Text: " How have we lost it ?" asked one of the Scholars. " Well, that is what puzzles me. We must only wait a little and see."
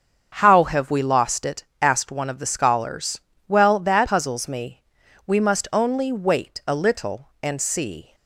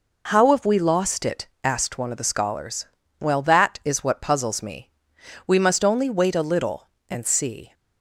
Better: second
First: skips "is what"; at 4.0 s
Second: none

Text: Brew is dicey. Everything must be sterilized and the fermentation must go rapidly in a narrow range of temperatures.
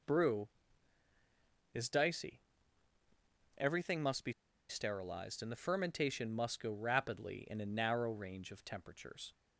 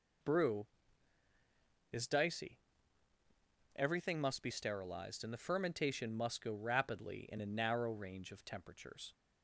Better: second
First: pauses between "be" and "sterilized"; at 4.3 s; 0.36 s long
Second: none

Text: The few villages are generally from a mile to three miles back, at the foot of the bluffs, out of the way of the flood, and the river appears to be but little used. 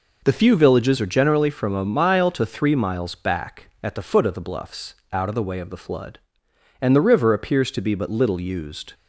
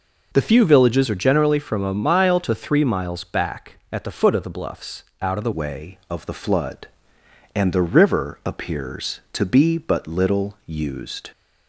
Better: first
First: none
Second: changes voice at "way"; from 5.5 s on; 5.7 s long

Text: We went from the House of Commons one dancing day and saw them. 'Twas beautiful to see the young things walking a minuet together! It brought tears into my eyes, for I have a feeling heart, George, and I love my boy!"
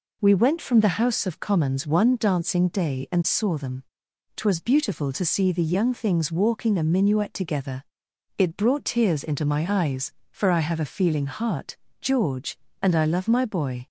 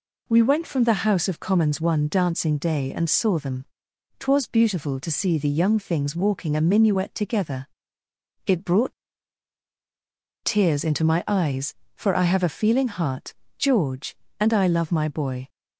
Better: first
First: none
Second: pauses between "brought" and "tears"; strong; at 8.9 s; 1.5 s long

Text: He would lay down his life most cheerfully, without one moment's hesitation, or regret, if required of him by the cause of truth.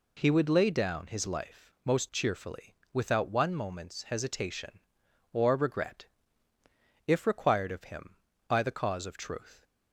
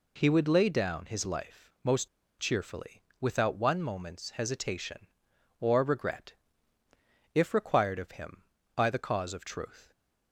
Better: first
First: pauses between "life" and "most"; slight; at 1.6 s; 0.16 s long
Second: pauses between "life" and "most"; slight; at 1.6 s; 0.16 s long // pauses between "most" and "cheerfully"; slight; at 2.0 s; 0.31 s long

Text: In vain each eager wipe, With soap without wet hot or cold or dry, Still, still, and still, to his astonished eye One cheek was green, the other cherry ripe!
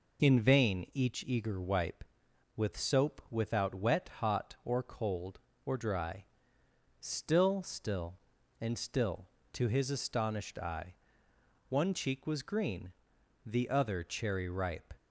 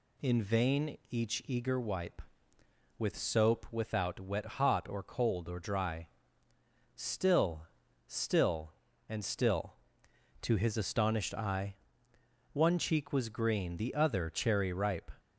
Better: neither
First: pauses between "eye" and "One"; noticeable; at 10.9 s; 0.76 s long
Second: pauses between "eye" and "One"; noticeable; at 11.7 s; 0.80 s long

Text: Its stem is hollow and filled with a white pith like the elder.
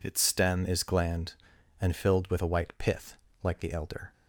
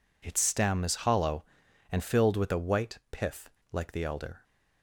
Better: second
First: says "gland" for "hollow"; at 0.8 s // pauses between "pith" and "like"; slight; at 3.1 s; 0.26 s long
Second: pauses between "pith" and "like"; slight; at 3.4 s; 0.22 s long

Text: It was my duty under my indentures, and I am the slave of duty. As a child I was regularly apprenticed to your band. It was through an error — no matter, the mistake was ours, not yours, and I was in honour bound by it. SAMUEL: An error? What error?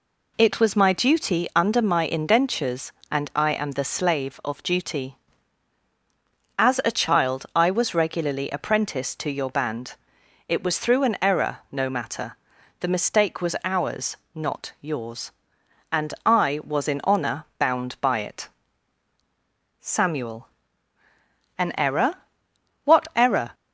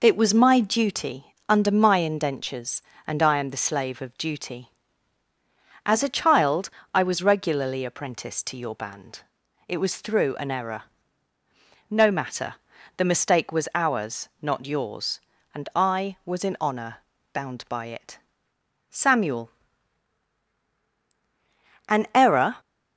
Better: first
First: pauses between "honour" and "bound"; slight; at 17.4 s; 0.16 s long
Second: pauses between "child" and "I"; slight; at 6.6 s; 0.24 s long // pauses between "honour" and "bound"; slight; at 16.9 s; 0.36 s long // stops before "What error"; at 22.5 s

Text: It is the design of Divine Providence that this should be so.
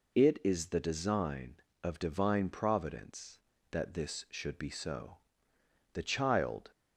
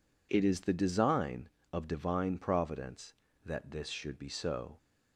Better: second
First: goes on to say "The child"; noticeable; from 5.9 s on; 0.78 s long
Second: none

